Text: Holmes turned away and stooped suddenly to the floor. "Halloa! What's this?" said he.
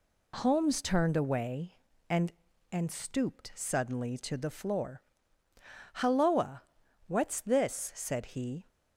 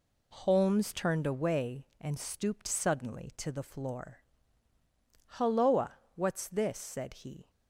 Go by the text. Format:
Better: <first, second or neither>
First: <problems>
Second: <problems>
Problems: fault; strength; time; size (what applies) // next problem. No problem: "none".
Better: second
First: says "and" twice; at 2.7 s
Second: none